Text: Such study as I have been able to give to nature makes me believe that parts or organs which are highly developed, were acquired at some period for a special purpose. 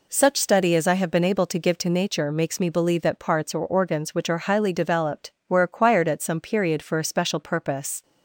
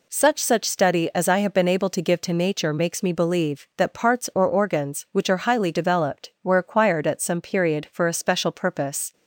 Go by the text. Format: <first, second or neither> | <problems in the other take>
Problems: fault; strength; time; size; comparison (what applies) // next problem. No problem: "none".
first | says "Such" twice; at 0.4 s